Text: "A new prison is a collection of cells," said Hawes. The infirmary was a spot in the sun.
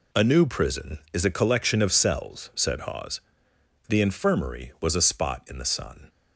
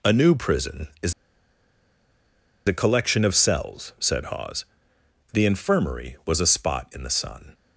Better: first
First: none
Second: pauses between "is" and "a"; strong; at 1.1 s; 1.5 s long

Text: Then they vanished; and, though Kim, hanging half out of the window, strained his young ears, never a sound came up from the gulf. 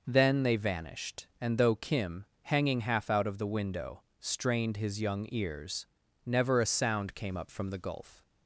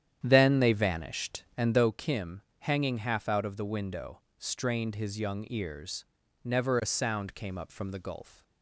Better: first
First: none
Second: starts louder than the rest; strong; until 1.9 s; 10 dB

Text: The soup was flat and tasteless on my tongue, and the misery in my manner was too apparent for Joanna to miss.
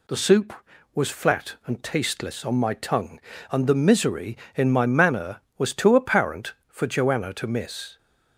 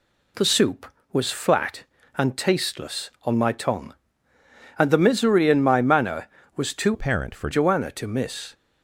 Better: first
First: none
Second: changes voice from "apparent" to "for"; from 6.9 to 7.4 s; 0.5 s long

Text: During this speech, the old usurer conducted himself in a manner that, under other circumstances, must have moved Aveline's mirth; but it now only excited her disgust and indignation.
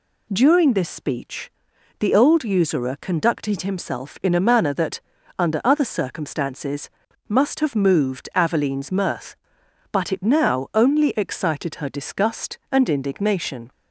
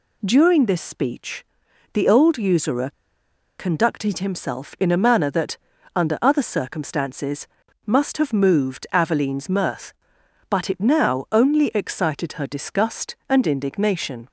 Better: first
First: none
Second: pauses between "usurer" and "conducted"; noticeable; at 2.9 s; 0.66 s long

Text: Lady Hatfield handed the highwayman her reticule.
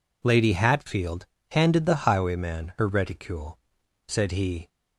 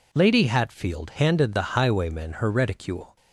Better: second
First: pauses between "Hatfield" and "handed"; slight; at 1.2 s; 0.24 s long // goes on to say "said he"; noticeable; from 4.0 s on; 0.62 s long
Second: none

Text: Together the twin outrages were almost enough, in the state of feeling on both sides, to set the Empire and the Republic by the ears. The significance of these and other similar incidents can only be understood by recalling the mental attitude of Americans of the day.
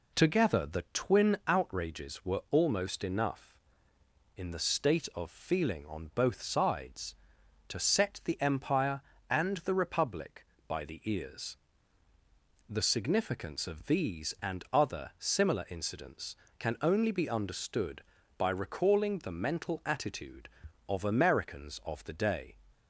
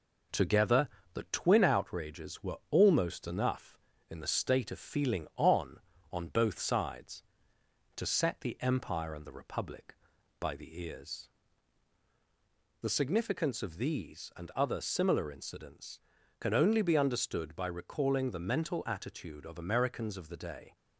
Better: first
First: none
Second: pauses between "Together" and "the"; slight; at 0.8 s; 0.26 s long // says "on" twice; at 6.1 s

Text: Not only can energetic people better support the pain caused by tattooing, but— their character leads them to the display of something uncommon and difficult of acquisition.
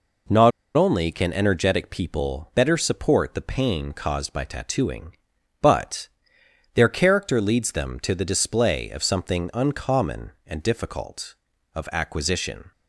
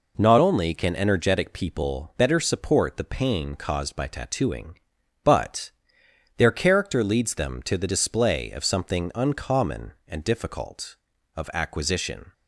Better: second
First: pauses between "Not" and "only"; slight; at 0.5 s; 0.24 s long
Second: none

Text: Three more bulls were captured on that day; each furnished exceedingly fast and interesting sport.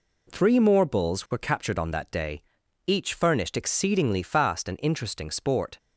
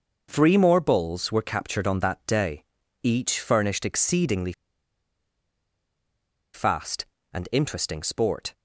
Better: first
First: none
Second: starts louder than the rest; noticeable; until 1.3 s; 6 dB // pauses between "exceedingly" and "fast"; strong; at 4.5 s; 2.0 s long

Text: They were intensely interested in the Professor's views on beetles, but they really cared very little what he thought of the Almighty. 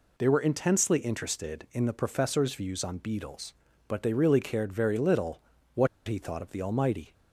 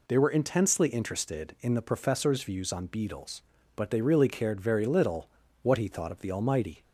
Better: second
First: pauses between "little" and "what"; slight; at 5.4 s; 0.34 s long // pauses between "what" and "he"; slight; at 5.8 s; 0.21 s long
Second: pauses between "little" and "what"; slight; at 5.2 s; 0.34 s long

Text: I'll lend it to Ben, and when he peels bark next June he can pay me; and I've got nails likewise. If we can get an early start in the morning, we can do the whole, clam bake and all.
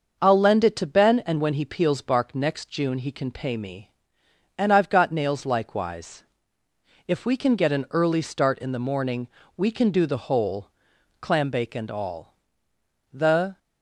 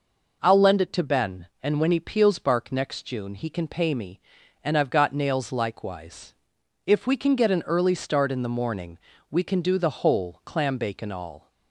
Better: second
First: starts louder than the rest; until 1.2 s; 6 dB // goes on to say "The"; slight; from 13.1 s on; 0.46 s long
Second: none

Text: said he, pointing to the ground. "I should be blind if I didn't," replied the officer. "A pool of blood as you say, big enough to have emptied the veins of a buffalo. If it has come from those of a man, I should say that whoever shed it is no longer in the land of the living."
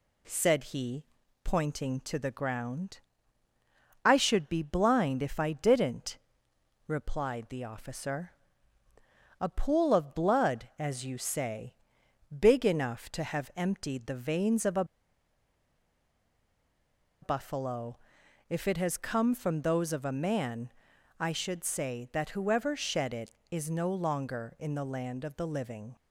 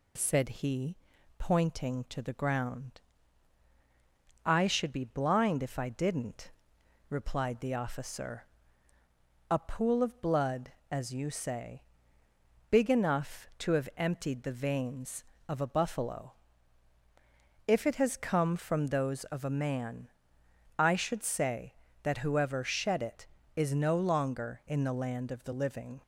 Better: second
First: pauses between "a" and "buffalo"; strong; at 14.8 s; 2.3 s long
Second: none

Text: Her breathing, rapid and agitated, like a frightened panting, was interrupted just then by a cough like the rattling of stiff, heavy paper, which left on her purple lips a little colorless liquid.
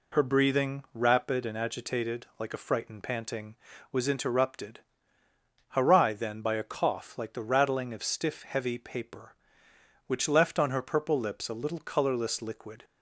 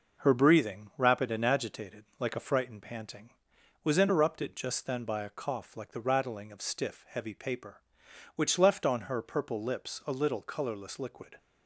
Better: second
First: says "harai" for "just"; at 5.7 s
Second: none

